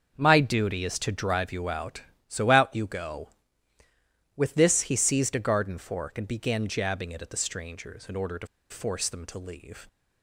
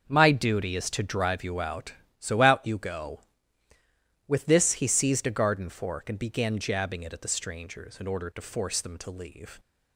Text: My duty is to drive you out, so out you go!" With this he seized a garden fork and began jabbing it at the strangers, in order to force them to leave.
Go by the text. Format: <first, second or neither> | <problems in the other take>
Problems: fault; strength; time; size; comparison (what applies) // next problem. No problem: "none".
second | starts louder than the rest; until 1.2 s; 6.5 dB; also in the second // pauses between "to" and "force"; slight; at 8.4 s; 0.23 s long